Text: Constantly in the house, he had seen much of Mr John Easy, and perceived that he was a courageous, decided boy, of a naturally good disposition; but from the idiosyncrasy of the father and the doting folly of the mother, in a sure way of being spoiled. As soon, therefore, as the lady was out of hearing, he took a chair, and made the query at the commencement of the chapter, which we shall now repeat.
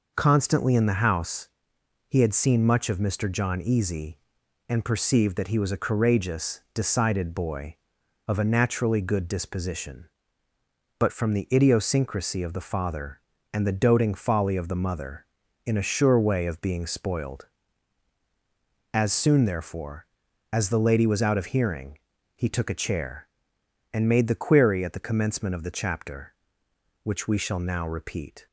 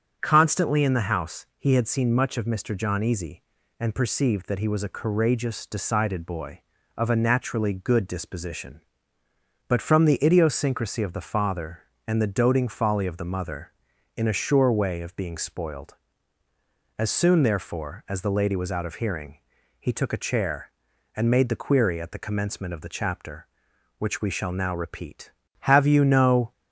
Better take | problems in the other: first | starts louder than the rest; until 1.2 s; 7 dB // goes on to say "Have you no"; noticeable; from 25.5 s on; 0.92 s long

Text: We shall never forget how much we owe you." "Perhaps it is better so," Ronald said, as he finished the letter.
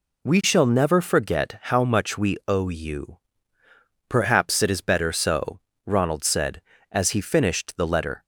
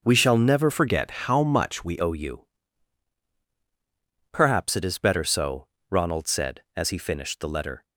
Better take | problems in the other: first | changes voice from "forget" to "we"; from 0.6 to 1.9 s; 1.3 s long

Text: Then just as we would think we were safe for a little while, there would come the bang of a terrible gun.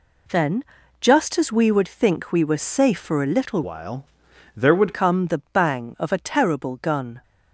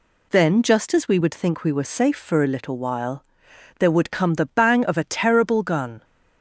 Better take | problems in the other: second | pauses between "Then" and "just"; slight; at 0.6 s; 0.36 s long // changes voice from "while" to "would"; from 3.6 to 4.9 s; 1.3 s long

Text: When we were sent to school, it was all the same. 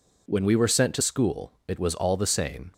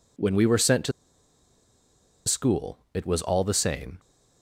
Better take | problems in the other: first | pauses between "to" and "school"; strong; at 0.9 s; 1.3 s long

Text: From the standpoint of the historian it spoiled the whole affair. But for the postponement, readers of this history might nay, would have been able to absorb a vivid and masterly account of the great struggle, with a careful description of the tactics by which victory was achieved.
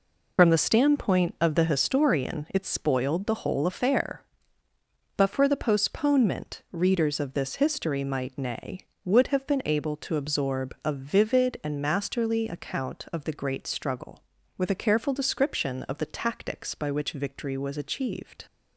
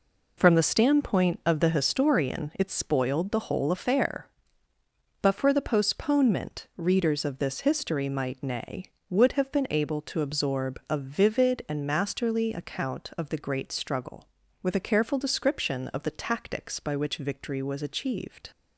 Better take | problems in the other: second | loses the start of "From"; at 0.3 s; 60 ms

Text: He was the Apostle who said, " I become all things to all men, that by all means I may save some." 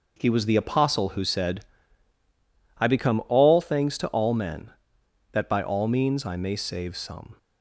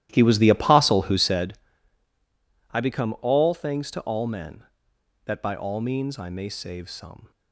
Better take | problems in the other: first | starts louder than the rest; strong; until 1.5 s; 13 dB

